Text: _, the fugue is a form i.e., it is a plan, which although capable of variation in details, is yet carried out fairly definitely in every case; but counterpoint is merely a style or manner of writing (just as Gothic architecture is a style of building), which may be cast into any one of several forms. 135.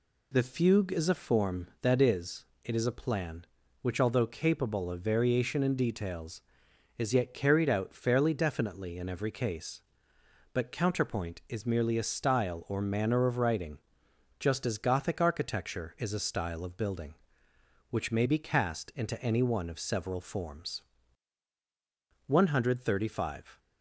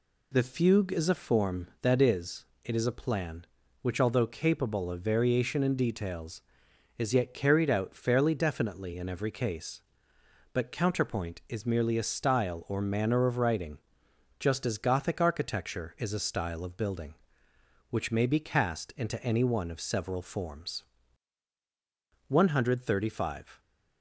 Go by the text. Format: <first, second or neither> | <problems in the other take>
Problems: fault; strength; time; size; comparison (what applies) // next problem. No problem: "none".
neither | none